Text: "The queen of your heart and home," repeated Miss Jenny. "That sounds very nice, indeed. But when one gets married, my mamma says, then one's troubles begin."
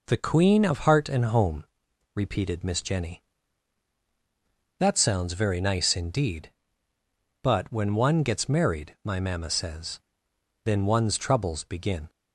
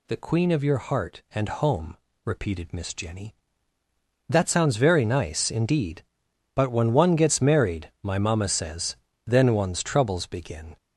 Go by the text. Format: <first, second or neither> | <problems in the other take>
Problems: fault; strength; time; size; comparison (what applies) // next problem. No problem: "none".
second | skips "your"; at 0.8 s